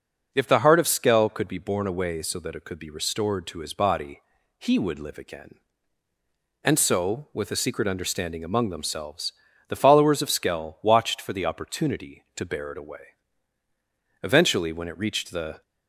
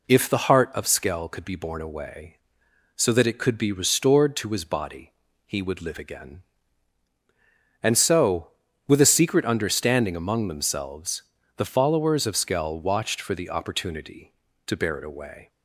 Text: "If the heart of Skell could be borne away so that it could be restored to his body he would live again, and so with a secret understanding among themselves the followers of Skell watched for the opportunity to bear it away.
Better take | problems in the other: second | pauses between "body" and "he"; at 4.2 s; 0.40 s long; slight in the second // pauses between "themselves" and "the"; at 9.3 s; 0.38 s long; slight in the second // goes on to say "Eventually when it reached the"; from 14.2 s on; 1.4 s long

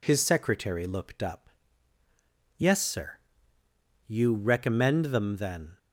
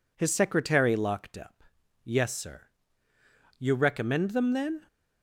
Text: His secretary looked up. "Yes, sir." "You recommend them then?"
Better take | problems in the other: first | says "locked" for "looked"; at 0.9 s

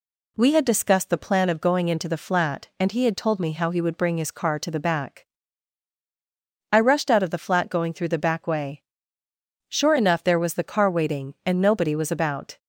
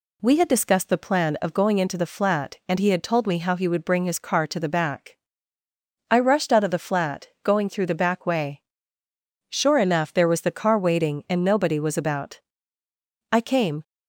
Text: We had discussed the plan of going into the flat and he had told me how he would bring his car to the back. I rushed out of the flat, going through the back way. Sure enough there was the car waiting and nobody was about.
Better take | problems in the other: first | goes on to say "I came"; from 13.3 s on; 0.50 s long

